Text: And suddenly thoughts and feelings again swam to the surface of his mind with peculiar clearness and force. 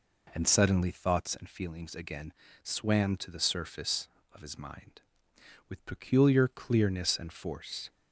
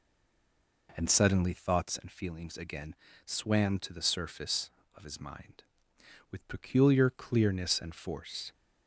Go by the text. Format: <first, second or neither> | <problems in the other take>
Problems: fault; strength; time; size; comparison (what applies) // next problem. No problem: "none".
first | stays silent before the first word; slight; until 0.8 s; 0.8 s long // pauses between "again" and "swam"; slight; at 2.9 s; 0.30 s long; slight in the first